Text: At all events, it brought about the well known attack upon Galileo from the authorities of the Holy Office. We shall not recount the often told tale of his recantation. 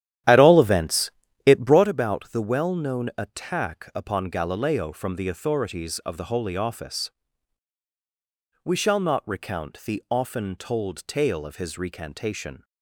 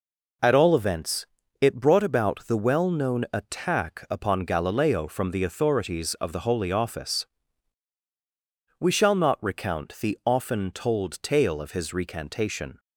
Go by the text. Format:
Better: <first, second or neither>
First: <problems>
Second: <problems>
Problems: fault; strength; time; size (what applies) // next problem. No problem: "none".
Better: second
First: starts louder than the rest; strong; until 2.0 s; 11.5 dB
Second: none